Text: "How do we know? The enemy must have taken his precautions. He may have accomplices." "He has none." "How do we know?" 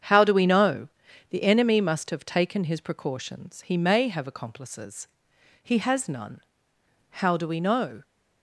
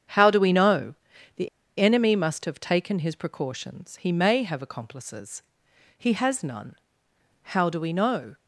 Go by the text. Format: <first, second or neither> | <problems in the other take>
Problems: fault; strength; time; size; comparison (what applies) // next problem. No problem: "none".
first | starts louder than the rest; strong; until 1.8 s; 8 dB; strong in the first // pauses between "The" and "enemy"; slight; at 1.4 s; 0.30 s long